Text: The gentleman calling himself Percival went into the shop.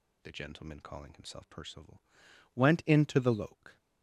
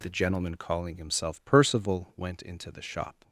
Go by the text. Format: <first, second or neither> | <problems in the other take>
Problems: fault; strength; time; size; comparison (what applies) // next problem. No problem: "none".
second | pauses between "Percival" and "went"; noticeable; at 2.0 s; 0.52 s long // says "loke" for "shop"; at 3.3 s